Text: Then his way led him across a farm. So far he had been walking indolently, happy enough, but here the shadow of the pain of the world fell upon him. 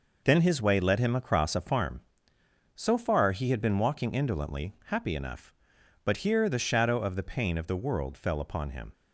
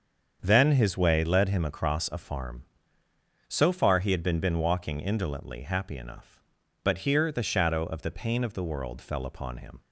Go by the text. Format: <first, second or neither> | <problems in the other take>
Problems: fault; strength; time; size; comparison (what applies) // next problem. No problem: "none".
first | starts louder than the rest; strong; until 1.4 s; 7 dB // says "been" twice; at 4.3 s